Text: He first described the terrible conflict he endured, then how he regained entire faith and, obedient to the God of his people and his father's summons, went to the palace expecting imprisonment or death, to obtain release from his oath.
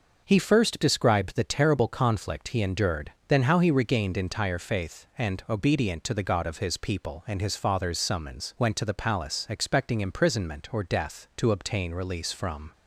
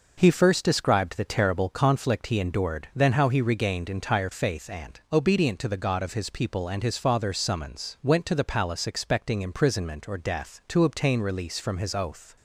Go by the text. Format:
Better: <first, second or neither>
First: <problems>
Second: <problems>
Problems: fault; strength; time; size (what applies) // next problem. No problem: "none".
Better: second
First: stops before "his oath"; at 12.7 s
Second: none